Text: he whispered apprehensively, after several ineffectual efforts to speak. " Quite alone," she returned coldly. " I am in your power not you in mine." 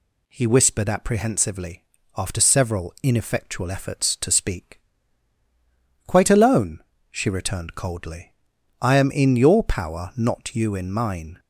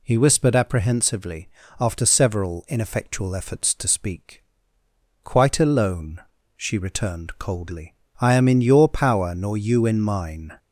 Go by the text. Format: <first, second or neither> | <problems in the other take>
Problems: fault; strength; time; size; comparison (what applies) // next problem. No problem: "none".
first | says "nor" for "not"; at 9.3 s